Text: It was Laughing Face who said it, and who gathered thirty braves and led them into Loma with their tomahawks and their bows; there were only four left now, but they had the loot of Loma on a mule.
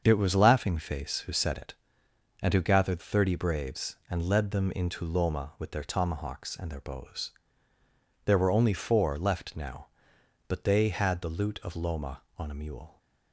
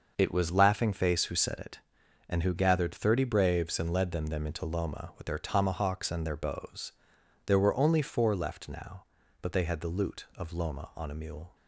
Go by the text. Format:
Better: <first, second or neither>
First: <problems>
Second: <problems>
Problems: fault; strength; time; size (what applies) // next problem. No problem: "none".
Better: first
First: starts louder than the rest; until 1.0 s; 7 dB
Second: starts louder than the rest; noticeable; until 1.1 s; 6 dB // says "them" twice; at 4.2 s